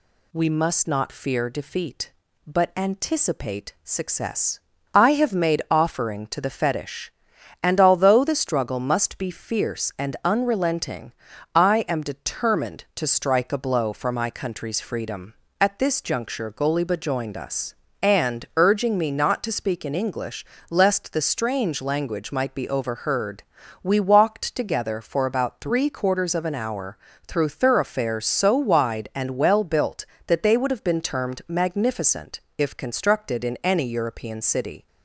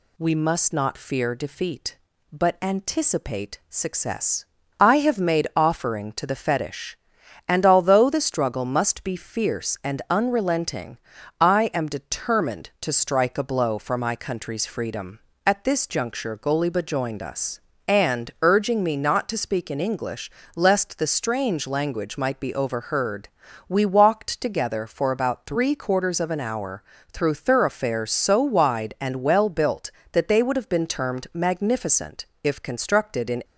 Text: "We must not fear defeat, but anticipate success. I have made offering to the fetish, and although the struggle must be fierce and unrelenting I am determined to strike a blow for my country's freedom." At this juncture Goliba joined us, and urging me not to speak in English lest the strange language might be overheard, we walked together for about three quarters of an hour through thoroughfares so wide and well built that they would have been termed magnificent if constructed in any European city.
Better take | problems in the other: first | pauses between "unrelenting" and "I"; at 10.9 s; 0.42 s long; also in the first // pauses between "English" and "lest"; slight; at 20.2 s; 0.28 s long; slight in the first // pauses between "hour" and "through"; slight; at 26.8 s; 0.30 s long; slight in the first // pauses between "magnificent" and "if"; slight; at 32.2 s; 0.16 s long; slight in the first // stops before "any European city"; at 33.4 s

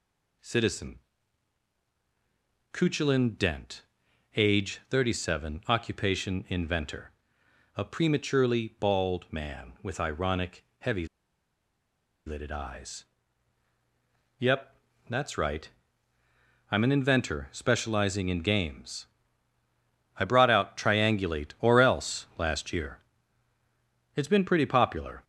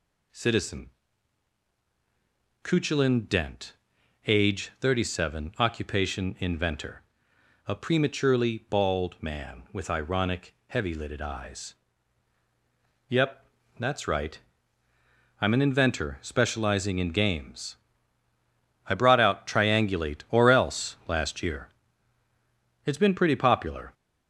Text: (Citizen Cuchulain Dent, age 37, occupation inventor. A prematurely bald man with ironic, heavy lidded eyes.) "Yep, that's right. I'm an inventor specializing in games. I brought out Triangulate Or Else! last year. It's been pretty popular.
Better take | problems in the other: second | pauses between "Citizen" and "Cuchulain"; strong; at 0.9 s; 1.7 s long; strong in the second // pauses between "heavy" and "lidded"; at 11.0 s; 1.2 s long

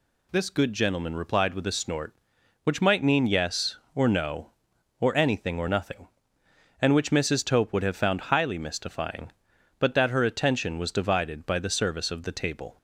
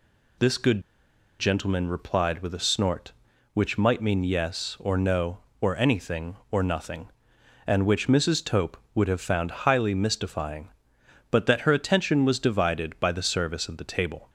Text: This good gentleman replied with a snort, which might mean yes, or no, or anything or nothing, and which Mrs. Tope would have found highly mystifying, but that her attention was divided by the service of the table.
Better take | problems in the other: first | pauses between "good" and "gentleman"; noticeable; at 0.8 s; 0.57 s long

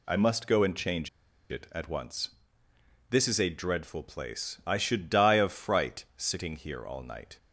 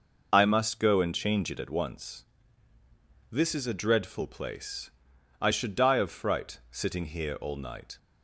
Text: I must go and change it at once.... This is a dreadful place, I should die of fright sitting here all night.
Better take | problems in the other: second | pauses between "change" and "it"; at 1.0 s; 0.42 s long

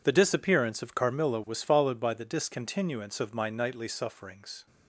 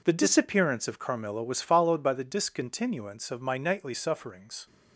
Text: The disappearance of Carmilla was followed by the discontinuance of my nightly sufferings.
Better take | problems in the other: neither | none

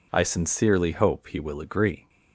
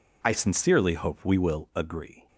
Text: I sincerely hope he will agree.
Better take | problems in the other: first | says "we" for "he"; at 1.2 s

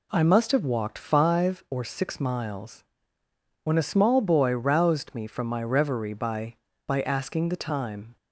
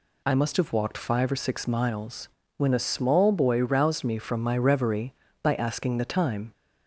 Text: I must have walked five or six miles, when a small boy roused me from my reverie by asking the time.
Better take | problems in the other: second | says "by" twice; at 6.8 s

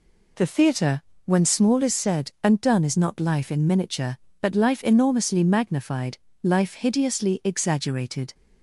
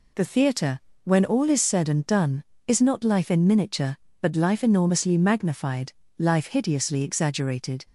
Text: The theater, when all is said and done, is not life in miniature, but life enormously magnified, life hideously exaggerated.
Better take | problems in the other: second | says "small" for "all"; at 1.4 s

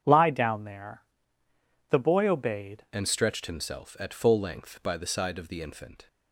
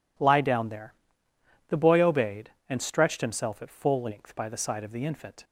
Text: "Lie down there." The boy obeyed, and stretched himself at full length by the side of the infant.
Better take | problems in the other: second | starts louder than the rest; strong; until 1.0 s; 8 dB // changes voice at "and"; from 2.9 s on; 3.1 s long

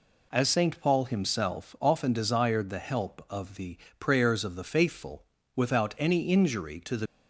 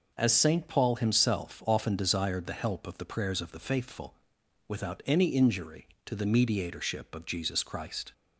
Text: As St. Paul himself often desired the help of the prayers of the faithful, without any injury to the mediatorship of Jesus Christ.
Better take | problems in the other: second | pauses between "the" and "prayers"; slight; at 3.7 s; 0.24 s long // stops before "mediatorship of Jesus Christ"; at 7.0 s

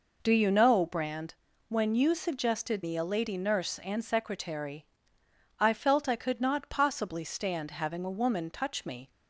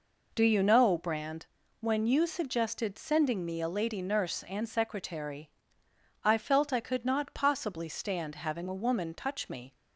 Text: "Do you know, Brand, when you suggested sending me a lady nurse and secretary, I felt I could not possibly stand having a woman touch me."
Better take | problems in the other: second | skips "sending"; at 2.8 s

